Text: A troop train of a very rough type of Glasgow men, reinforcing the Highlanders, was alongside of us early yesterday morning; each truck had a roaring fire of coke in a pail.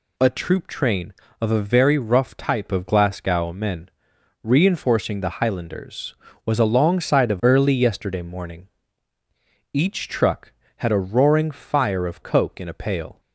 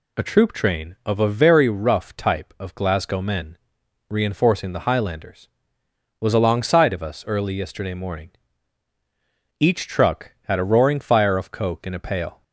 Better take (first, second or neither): second